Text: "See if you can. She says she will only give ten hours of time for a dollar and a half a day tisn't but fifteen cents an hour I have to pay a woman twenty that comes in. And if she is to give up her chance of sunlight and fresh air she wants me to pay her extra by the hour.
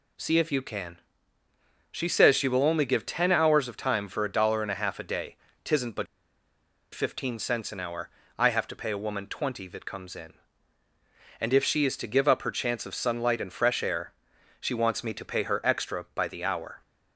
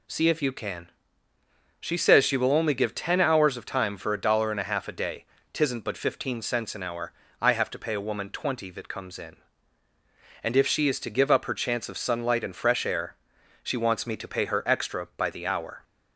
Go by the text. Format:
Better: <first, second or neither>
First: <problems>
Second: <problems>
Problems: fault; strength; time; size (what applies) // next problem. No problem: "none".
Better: second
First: pauses between "day" and "tisn't"; slight; at 5.3 s; 0.28 s long // pauses between "but" and "fifteen"; noticeable; at 6.0 s; 0.88 s long // pauses between "hour" and "I"; slight; at 8.0 s; 0.28 s long // pauses between "air" and "she"; noticeable; at 14.1 s; 0.48 s long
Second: pauses between "day" and "tisn't"; slight; at 5.2 s; 0.28 s long // pauses between "hour" and "I"; slight; at 7.1 s; 0.28 s long // pauses between "air" and "she"; noticeable; at 13.1 s; 0.48 s long